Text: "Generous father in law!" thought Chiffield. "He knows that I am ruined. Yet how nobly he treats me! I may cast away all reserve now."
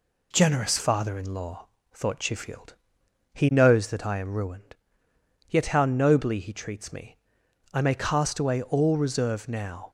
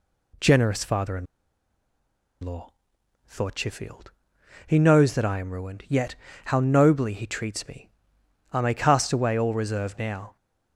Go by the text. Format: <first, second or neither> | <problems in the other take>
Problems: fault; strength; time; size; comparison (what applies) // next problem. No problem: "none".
first | pauses between "in" and "law"; at 1.2 s; 1.1 s long // pauses between "Yet" and "how"; slight; at 6.1 s; 0.32 s long